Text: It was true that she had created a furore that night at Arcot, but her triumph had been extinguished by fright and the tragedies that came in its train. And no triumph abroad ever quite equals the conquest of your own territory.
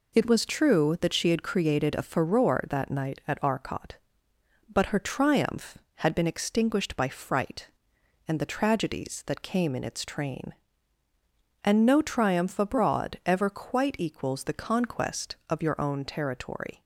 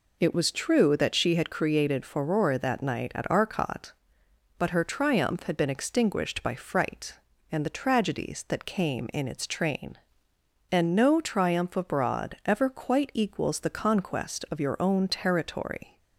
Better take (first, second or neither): first